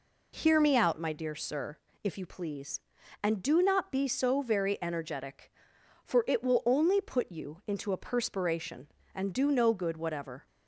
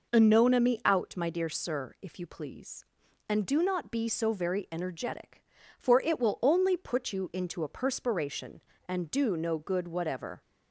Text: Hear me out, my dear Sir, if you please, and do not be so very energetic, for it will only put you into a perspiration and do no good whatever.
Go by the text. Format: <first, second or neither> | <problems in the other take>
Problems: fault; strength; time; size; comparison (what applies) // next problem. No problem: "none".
first | says "Anona" for "Hear"; at 0.1 s